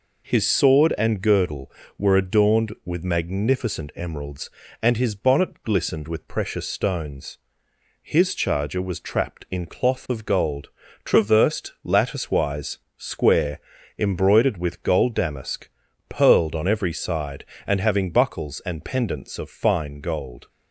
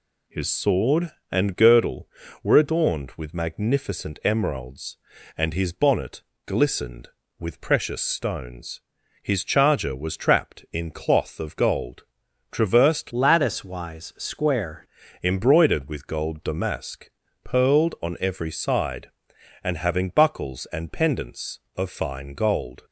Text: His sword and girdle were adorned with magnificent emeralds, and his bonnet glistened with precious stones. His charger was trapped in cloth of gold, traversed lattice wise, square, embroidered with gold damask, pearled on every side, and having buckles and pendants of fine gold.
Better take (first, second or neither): first